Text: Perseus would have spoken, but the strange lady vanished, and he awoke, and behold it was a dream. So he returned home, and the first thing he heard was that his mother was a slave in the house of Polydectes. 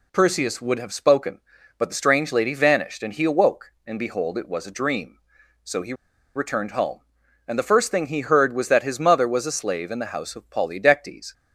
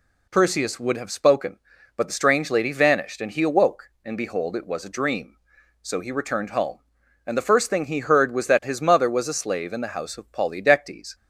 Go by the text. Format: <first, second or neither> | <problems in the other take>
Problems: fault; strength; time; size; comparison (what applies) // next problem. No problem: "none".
second | pauses between "he" and "returned"; at 5.9 s; 0.42 s long